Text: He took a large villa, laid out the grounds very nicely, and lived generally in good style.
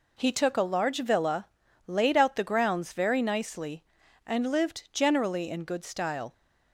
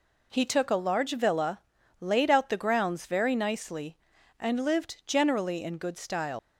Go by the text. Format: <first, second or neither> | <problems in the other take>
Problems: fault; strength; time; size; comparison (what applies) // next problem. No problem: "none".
first | leaves "style" unfinished; at 6.3 s; 70 ms